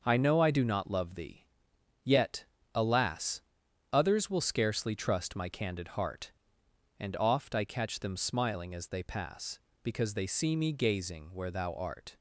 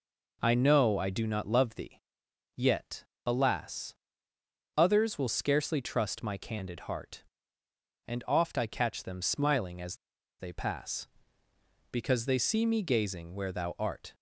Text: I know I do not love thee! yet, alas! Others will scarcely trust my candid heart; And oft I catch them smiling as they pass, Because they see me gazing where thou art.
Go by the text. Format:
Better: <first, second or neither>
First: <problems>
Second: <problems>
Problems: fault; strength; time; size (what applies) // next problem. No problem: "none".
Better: first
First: none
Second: pauses between "as" and "they"; at 9.9 s; 0.43 s long